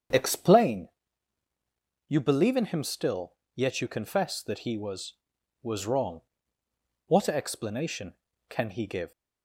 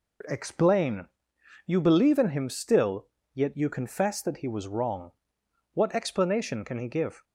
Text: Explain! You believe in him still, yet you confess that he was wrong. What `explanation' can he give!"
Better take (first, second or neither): second